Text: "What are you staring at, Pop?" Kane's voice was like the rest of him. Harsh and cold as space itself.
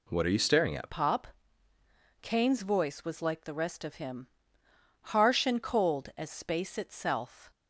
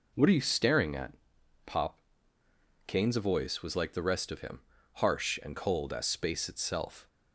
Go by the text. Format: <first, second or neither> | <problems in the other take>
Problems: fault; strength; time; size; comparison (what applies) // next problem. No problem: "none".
second | changes voice at "Pop"; from 0.8 s on; 6.7 s long